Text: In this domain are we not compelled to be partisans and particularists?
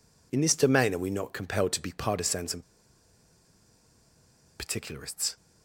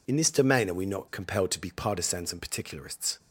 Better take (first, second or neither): second